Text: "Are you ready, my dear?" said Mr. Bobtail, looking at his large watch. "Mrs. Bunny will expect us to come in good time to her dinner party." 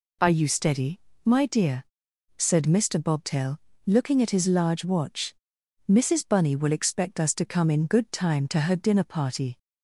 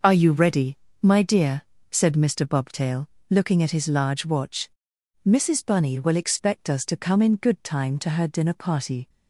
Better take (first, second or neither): second